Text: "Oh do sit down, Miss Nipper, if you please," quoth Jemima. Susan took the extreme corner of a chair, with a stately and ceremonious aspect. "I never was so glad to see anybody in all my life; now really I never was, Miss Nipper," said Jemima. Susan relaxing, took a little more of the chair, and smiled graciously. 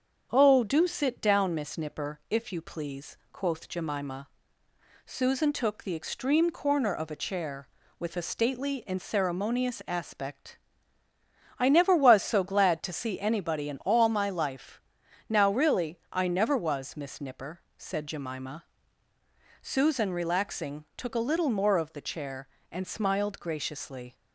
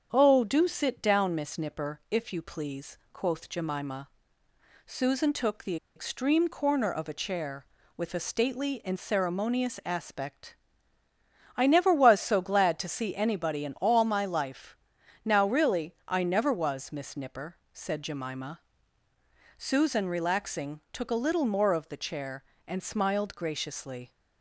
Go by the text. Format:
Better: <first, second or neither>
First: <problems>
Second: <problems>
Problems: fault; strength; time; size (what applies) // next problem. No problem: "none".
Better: first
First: starts louder than the rest; strong; until 1.3 s; 7 dB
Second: starts louder than the rest; strong; until 1.1 s; 7 dB // pauses between "the" and "extreme"; slight; at 5.7 s; 0.20 s long